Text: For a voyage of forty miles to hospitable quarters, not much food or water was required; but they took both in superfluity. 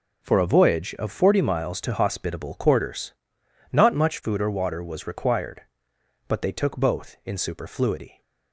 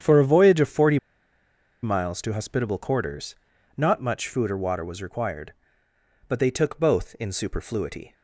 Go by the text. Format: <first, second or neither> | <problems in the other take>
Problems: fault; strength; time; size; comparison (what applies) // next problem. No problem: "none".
first | starts louder than the rest; strong; until 1.8 s; 8.5 dB // pauses between "forty" and "miles"; noticeable; at 0.9 s; 0.85 s long